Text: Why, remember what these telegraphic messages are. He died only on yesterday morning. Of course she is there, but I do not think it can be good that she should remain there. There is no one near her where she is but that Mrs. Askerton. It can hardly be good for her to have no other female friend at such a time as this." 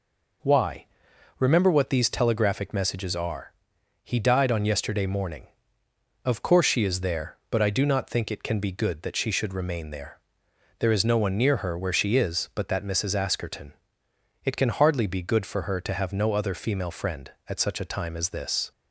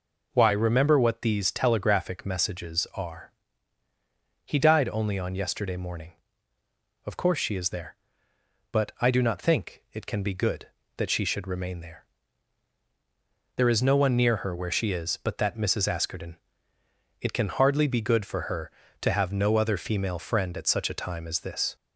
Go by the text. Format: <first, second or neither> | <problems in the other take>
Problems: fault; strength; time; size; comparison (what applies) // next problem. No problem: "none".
second | skips "only"; at 4.4 s